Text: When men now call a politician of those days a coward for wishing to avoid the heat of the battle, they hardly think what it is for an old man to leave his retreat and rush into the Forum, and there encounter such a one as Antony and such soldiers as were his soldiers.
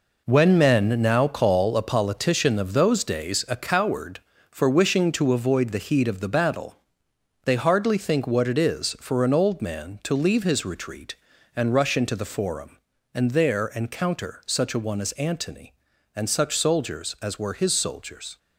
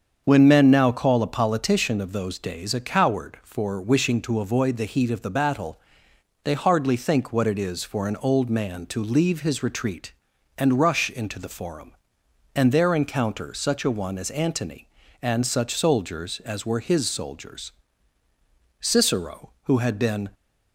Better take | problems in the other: first | starts louder than the rest; strong; until 1.2 s; 7 dB // goes on to say "Cicero who had been"; from 18.8 s on; 1.5 s long

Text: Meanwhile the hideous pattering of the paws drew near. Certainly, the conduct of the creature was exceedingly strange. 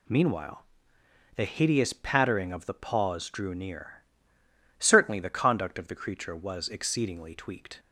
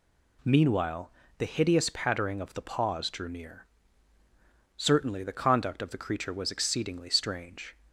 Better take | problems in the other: second | pauses between "Meanwhile" and "the"; noticeable; at 0.6 s; 0.72 s long; slight in the second // says "tweaked" for "strange"; at 7.3 s

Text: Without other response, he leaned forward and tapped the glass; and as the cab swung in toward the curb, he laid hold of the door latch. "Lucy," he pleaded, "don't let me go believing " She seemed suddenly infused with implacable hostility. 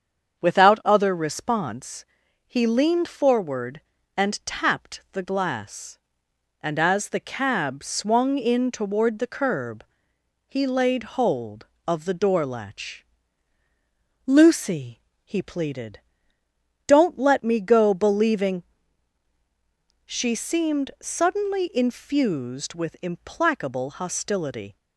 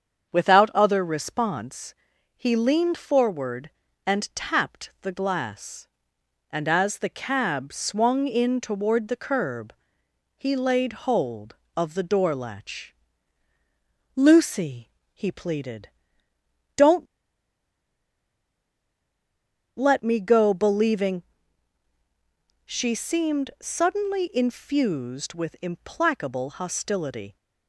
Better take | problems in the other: first | starts louder than the rest; strong; until 1.3 s; 7.5 dB; strong in the first // pauses between "don't" and "let"; strong; at 17.0 s; 2.7 s long

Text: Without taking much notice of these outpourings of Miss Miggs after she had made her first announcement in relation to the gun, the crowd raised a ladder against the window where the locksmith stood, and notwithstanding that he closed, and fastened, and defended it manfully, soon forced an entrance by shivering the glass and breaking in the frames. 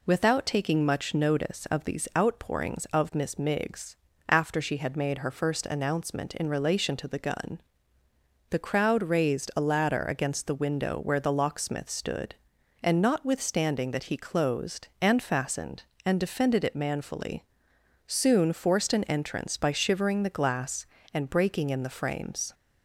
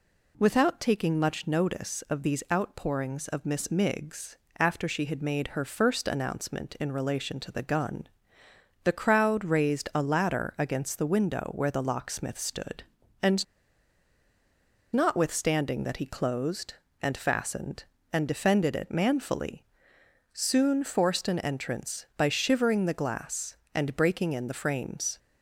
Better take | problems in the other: first | pauses between "Miggs" and "after"; slight; at 4.3 s; 0.22 s long; slight in the first // pauses between "and" and "notwithstanding"; strong; at 13.4 s; 1.4 s long

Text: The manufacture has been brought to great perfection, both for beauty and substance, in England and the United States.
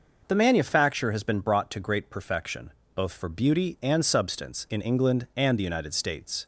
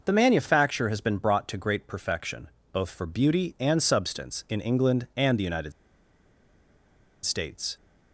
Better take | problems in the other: first | pauses between "United" and "States"; strong; at 5.7 s; 1.5 s long

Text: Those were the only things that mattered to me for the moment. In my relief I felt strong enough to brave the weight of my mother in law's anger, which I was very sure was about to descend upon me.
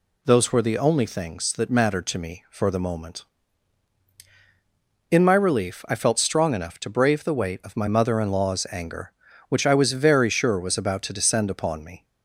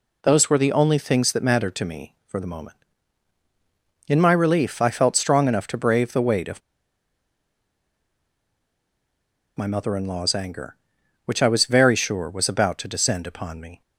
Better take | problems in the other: first | pauses between "of" and "my"; strong; at 6.6 s; 2.9 s long

